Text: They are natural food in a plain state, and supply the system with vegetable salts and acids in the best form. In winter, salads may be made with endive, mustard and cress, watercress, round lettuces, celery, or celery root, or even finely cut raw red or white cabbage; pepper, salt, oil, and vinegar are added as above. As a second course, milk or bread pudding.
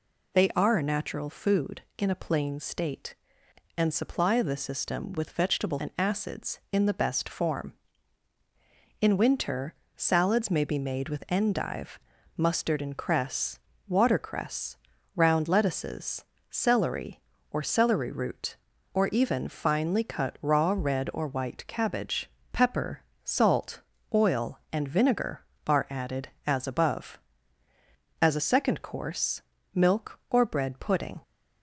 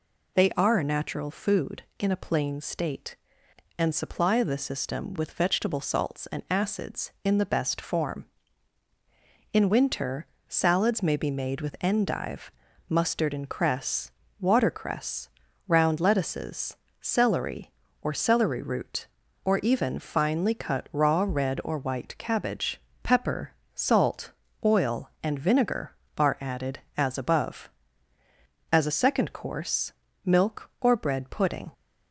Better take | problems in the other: second | skips "salts"; at 5.7 s

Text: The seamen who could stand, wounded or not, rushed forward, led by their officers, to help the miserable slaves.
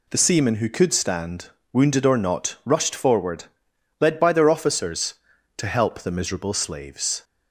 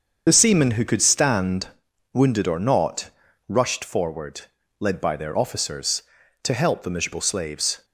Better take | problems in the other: first | loses the start of "The"; at 0.2 s; 35 ms // starts louder than the rest; until 1.2 s; 7 dB

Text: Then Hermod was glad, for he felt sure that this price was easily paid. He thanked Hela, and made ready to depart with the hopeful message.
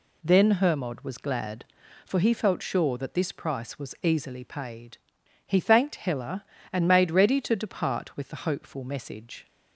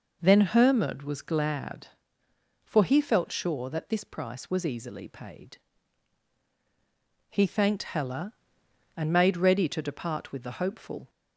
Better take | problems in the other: first | stops before "message"; at 11.0 s

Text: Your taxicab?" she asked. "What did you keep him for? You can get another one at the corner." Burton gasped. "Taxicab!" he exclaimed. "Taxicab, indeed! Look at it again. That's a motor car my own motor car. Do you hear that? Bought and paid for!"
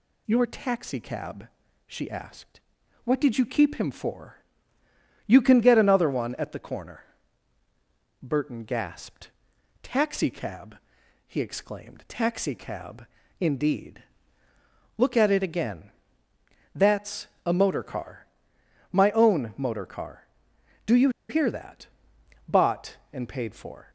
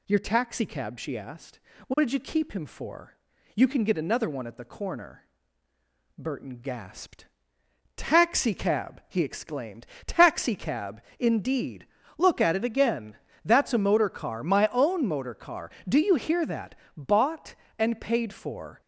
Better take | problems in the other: second | pauses between "That's" and "a"; slight; at 17.2 s; 0.18 s long // pauses between "car" and "my"; noticeable; at 18.2 s; 0.66 s long // pauses between "you" and "hear"; slight; at 21.0 s; 0.20 s long

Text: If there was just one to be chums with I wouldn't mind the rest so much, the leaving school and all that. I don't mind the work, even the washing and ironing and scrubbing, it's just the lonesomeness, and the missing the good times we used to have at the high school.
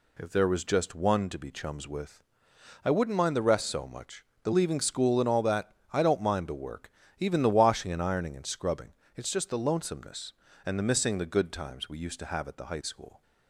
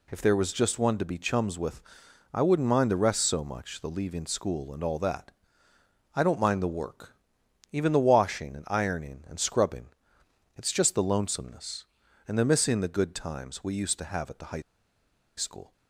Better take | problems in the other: first | pauses between "with" and "I"; noticeable; at 1.8 s; 0.50 s long; noticeable in the first // pauses between "high" and "school"; noticeable; at 14.6 s; 0.75 s long

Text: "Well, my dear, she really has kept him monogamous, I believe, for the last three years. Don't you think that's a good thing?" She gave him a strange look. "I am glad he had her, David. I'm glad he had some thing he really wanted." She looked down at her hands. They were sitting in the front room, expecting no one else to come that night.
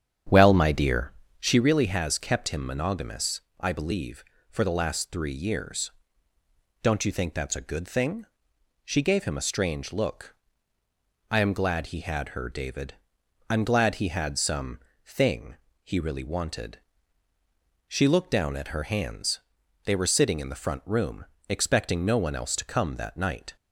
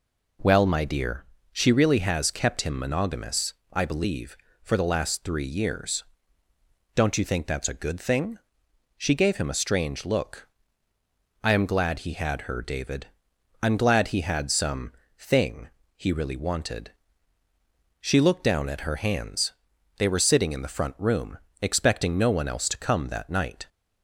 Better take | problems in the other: second | starts louder than the rest; strong; until 1.6 s; 8.5 dB // pauses between "some" and "thing"; slight; at 14.7 s; 0.26 s long; slight in the second // pauses between "thing" and "he"; slight; at 15.5 s; 0.28 s long; slight in the second

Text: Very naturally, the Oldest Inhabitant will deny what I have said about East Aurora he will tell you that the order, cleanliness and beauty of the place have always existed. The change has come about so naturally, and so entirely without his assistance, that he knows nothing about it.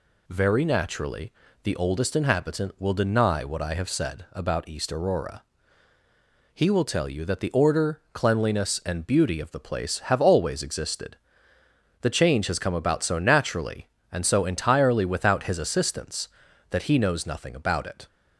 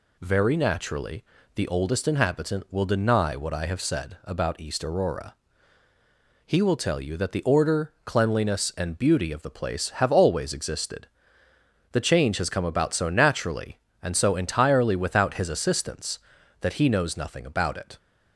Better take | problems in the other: neither | pauses between "Aurora" and "he"; the same in both

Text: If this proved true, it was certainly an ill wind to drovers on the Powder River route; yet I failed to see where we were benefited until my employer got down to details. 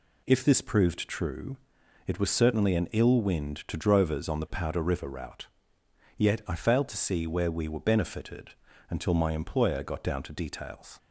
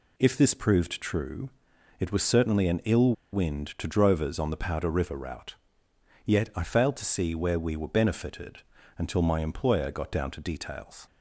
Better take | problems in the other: first | pauses between "ill" and "wind"; slight; at 3.1 s; 0.20 s long // pauses between "benefited" and "until"; slight; at 8.6 s; 0.34 s long; slight in the first

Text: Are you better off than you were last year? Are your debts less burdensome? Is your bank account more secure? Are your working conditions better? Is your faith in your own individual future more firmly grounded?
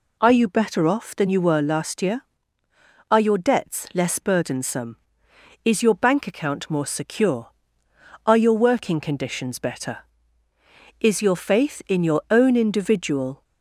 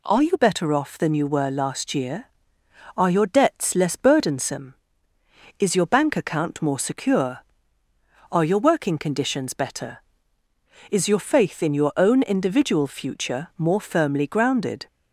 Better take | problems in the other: second | stops before "future more firmly grounded"; at 13.4 s

